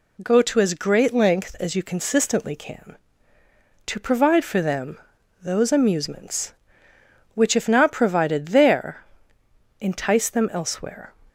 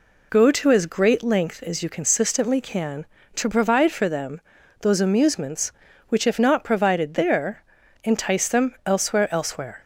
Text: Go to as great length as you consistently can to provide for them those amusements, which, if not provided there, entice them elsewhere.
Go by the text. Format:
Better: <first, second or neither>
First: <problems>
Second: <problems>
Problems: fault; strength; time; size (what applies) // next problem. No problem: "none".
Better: first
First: pauses between "them" and "those"; at 4.9 s; 0.42 s long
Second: pauses between "them" and "those"; at 4.4 s; 0.40 s long // says "elsewhere" twice; at 9.3 s